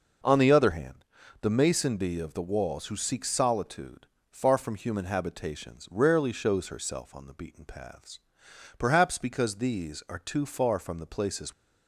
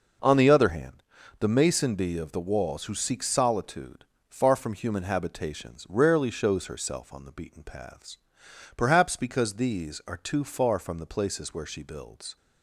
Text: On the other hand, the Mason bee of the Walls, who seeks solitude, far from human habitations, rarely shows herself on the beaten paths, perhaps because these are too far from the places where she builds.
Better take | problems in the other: second | stops before "where she builds"; at 11.5 s

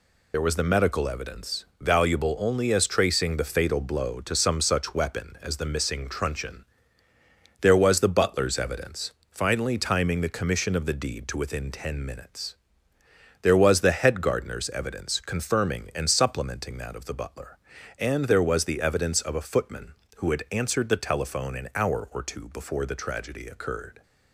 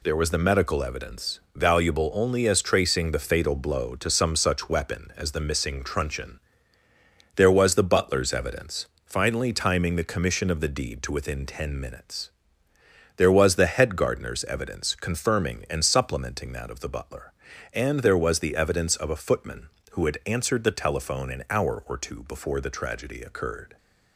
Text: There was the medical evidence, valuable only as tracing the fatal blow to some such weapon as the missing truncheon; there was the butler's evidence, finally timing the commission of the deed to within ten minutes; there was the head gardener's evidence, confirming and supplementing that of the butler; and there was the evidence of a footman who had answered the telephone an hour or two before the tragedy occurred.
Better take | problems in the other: second | loses the start of "There"; at 0.3 s; 75 ms

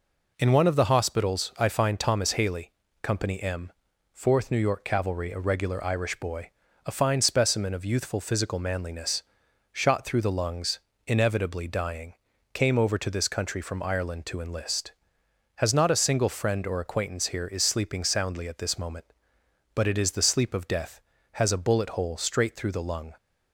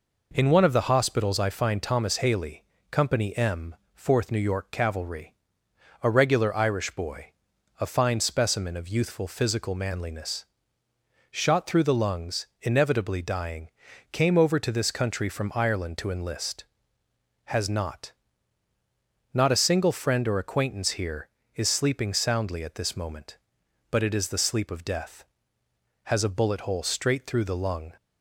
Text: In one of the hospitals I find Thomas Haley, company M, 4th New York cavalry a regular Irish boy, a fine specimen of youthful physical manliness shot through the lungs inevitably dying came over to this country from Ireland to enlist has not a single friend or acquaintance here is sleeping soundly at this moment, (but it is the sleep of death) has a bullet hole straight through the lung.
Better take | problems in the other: first | pauses between "cavalry" and "a"; noticeable; at 5.3 s; 0.70 s long // pauses between "manliness" and "shot"; noticeable; at 10.4 s; 0.84 s long; noticeable in the first // pauses between "lungs" and "inevitably"; slight; at 12.4 s; 0.16 s long; slight in the first // pauses between "dying" and "came"; at 13.6 s; 0.44 s long; also in the first // says "not" twice; at 19.3 s

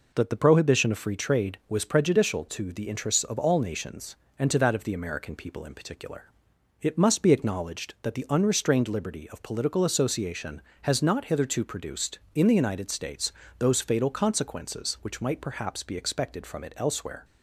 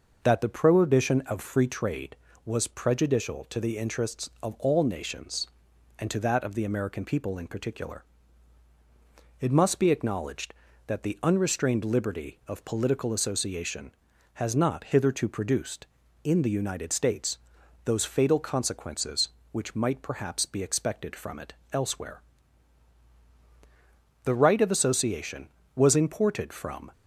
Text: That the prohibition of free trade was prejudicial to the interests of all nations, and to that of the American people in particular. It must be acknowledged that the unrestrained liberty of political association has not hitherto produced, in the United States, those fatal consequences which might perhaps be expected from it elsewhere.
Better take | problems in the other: first | pauses between "it" and "elsewhere"; slight; at 21.5 s; 0.18 s long // goes on to say "The right of association was imported from"; strong; from 24.2 s on; 2.6 s long

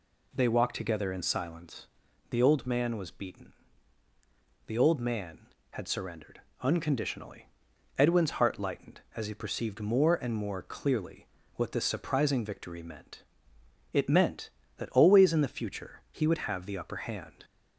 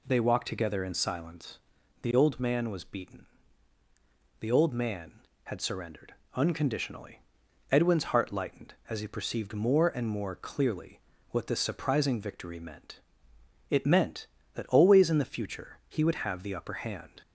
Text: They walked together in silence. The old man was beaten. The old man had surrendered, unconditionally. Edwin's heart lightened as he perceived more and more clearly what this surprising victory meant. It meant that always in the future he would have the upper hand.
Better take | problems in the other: neither | pauses between "clearly" and "what"; slight; the same in both

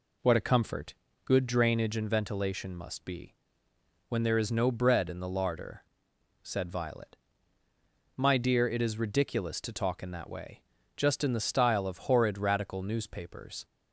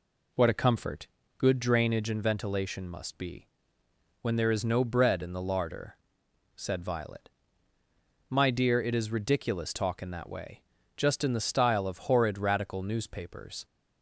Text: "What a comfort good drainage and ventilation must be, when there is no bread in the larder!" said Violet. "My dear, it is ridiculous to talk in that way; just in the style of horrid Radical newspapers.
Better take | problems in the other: first | pauses between "comfort" and "good"; slight; at 1.0 s; 0.28 s long; slight in the first // skips "to"; at 9.7 s

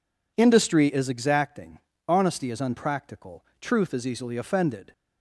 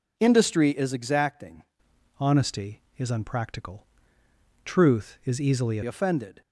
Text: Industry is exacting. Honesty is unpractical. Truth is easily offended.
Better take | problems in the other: first | changes voice from "Honesty" to "easily"; from 2.1 to 5.7 s; 3.6 s long

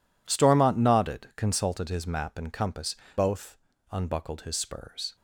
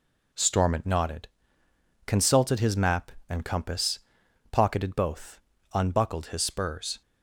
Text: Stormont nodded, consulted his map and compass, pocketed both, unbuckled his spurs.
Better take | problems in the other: second | skips "pocketed"; at 3.0 s

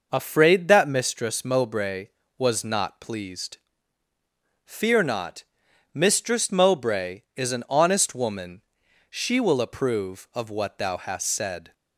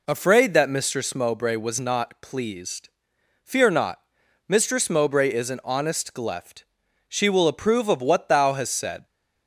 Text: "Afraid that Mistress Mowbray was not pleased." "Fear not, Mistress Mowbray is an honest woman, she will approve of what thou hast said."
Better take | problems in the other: first | says "gleft" for "woman"; at 6.1 s

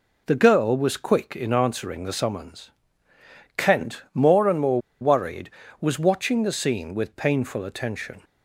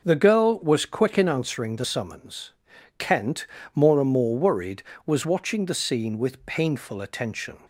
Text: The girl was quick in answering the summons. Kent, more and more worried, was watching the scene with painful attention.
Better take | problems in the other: second | pauses between "more" and "worried"; slight; at 4.7 s; 0.21 s long

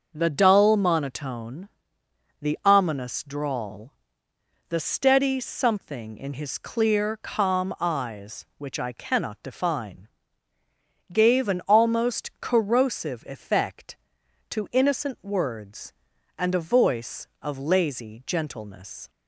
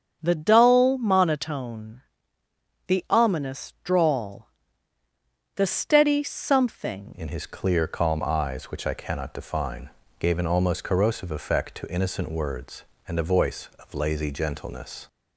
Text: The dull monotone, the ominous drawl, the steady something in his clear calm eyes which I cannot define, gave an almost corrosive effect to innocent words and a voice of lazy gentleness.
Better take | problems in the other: first | starts louder than the rest; strong; until 1.2 s; 7.5 dB; also in the first // changes voice at "in"; from 7.1 s on; 7.9 s long

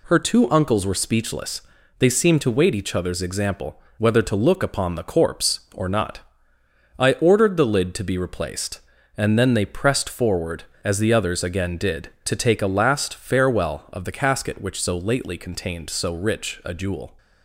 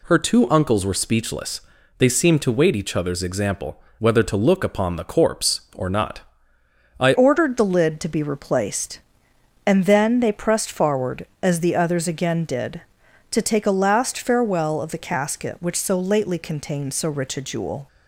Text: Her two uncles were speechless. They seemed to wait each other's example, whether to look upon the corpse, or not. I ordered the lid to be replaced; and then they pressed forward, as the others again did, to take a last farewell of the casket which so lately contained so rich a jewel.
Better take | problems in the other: first | changes voice at "ordered"; from 7.1 s on; 10.7 s long

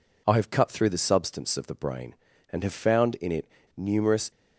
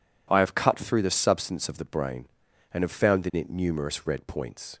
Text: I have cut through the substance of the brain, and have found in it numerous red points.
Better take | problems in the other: second | pauses between "it" and "numerous"; slight; at 3.4 s; 0.28 s long // stops before "red points"; at 4.3 s

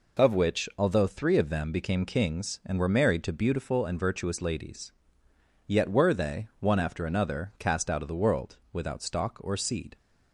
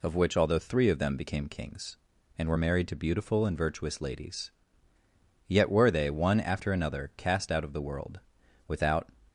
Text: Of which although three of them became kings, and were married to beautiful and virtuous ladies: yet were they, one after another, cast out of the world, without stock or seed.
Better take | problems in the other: first | stops before "stock or seed"; at 9.2 s

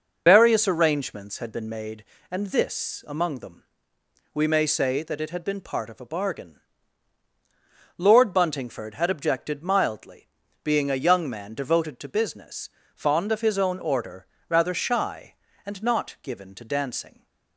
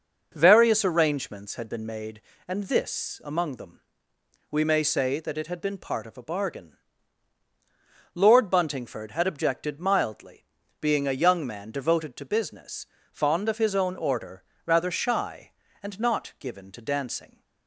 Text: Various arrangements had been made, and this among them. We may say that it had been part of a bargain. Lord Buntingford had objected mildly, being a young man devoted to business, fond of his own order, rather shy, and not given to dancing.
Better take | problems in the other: second | loses the start of "Various"; at 0.2 s; 115 ms

